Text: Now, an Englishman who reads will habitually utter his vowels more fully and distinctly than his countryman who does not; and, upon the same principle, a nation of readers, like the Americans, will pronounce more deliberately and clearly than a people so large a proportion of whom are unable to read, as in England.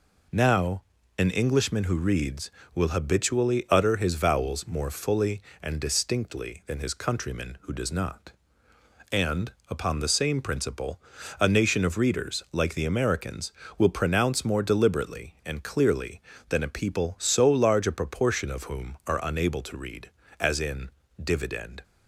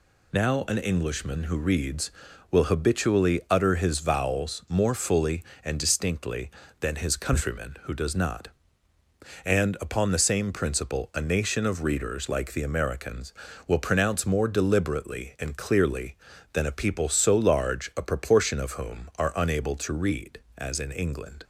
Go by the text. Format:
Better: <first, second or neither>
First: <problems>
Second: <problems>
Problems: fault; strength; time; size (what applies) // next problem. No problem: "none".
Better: second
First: says "Dividend" for "England"; at 21.2 s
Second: none